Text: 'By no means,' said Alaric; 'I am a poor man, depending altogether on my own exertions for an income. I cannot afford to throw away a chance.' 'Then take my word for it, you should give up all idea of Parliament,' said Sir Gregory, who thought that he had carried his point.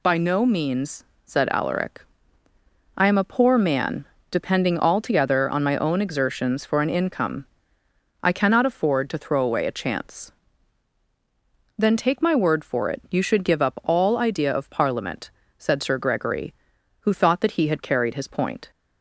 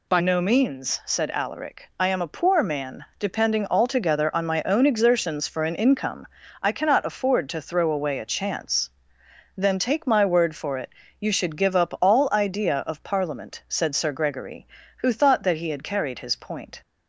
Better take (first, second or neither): first